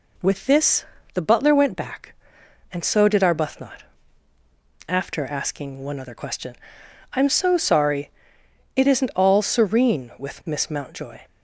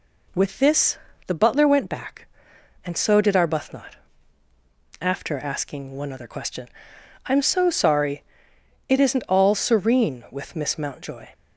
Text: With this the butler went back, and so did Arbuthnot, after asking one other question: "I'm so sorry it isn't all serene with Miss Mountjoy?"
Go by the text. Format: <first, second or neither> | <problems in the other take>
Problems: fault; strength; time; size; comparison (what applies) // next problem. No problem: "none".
neither | pauses between "this" and "the"; slight; the same in both // pauses between "sorry" and "it"; noticeable; the same in both